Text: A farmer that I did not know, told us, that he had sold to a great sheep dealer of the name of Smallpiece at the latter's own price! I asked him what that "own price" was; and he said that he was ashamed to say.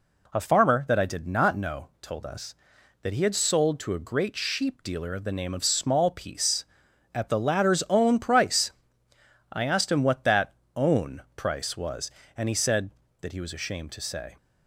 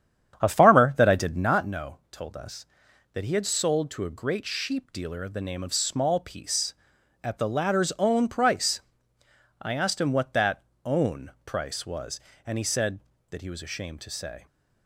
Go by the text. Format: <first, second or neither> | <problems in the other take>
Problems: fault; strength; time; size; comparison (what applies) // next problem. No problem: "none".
first | starts louder than the rest; strong; until 1.5 s; 9 dB // pauses between "that" and "own"; slight; at 10.6 s; 0.22 s long; slight in the first